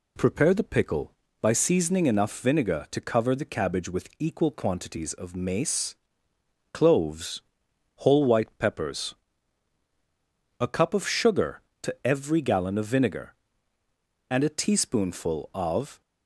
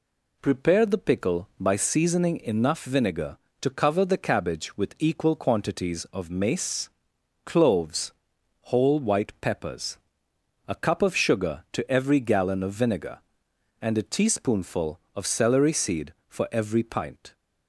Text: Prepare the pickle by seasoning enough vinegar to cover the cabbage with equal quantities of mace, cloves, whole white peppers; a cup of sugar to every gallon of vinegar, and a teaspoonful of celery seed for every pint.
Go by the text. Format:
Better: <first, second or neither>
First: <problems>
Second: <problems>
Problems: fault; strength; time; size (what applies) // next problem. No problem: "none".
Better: second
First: stops before "celery seed for every pint"; at 16.0 s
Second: none